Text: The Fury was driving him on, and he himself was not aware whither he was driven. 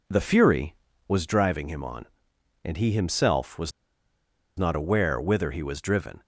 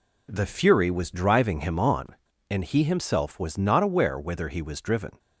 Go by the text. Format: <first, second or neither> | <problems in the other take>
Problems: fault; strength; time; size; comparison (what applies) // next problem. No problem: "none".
second | pauses between "was" and "not"; noticeable; at 3.7 s; 0.86 s long